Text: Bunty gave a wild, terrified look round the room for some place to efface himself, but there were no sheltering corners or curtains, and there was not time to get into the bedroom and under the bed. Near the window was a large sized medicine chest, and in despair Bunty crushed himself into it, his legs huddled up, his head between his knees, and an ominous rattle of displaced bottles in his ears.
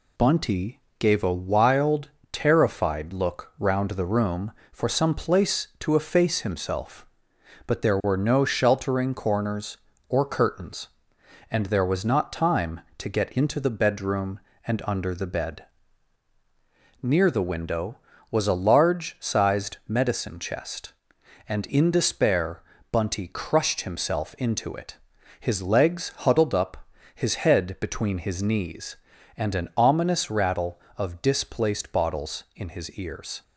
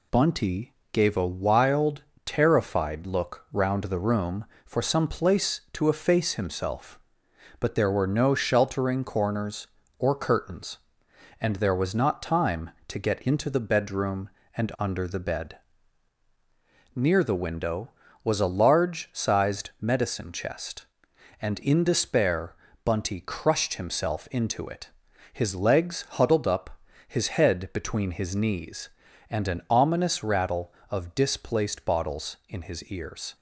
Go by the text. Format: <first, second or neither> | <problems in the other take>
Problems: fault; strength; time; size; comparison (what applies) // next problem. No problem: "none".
neither | pauses between "Bunty" and "gave"; slight; the same in both // pauses between "despair" and "Bunty"; slight; the same in both